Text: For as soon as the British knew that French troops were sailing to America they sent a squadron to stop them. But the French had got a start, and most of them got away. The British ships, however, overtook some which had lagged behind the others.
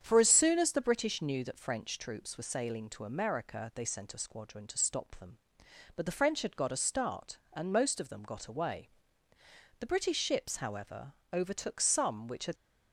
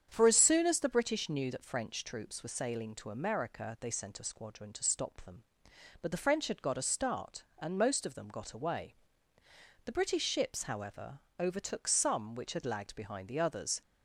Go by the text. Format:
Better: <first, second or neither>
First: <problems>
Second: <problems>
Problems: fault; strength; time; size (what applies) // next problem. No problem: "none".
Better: second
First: starts louder than the rest; strong; until 1.0 s; 8.5 dB // stops before "lagged behind the others"; at 12.5 s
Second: starts louder than the rest; strong; until 1.1 s; 8.5 dB